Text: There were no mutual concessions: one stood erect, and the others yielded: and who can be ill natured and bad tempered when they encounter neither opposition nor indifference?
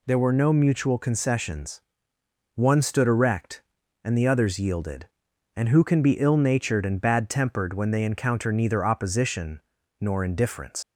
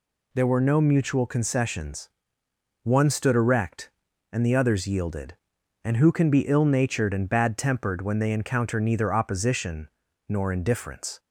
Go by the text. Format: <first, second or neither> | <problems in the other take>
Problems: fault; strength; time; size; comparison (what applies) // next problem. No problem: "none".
second | pauses between "opposition" and "nor"; at 9.6 s; 0.40 s long; also in the second // leaves "indifference" unfinished; at 10.8 s; 80 ms